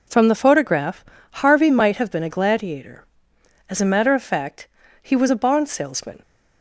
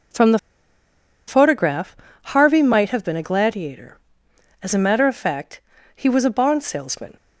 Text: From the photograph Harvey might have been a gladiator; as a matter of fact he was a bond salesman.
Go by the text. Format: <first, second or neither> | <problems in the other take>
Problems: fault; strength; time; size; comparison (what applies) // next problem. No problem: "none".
first | pauses between "the" and "photograph"; noticeable; at 0.3 s; 0.89 s long // pauses between "photograph" and "Harvey"; slight; at 1.9 s; 0.28 s long; slight in the first // pauses between "fact" and "he"; slight; at 5.6 s; 0.34 s long; slight in the first